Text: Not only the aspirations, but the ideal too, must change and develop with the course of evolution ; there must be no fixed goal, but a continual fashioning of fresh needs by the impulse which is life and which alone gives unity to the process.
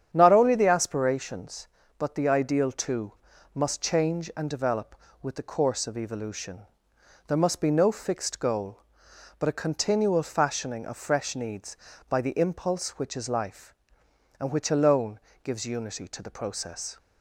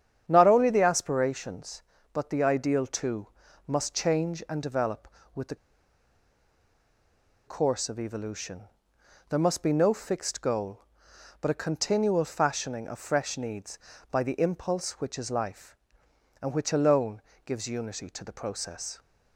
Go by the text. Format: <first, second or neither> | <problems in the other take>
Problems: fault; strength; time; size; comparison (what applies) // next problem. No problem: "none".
first | starts louder than the rest; strong; until 1.2 s; 9 dB; strong in the first // pauses between "the" and "course"; strong; at 5.5 s; 1.9 s long // pauses between "alone" and "gives"; slight; at 17.2 s; 0.24 s long; slight in the first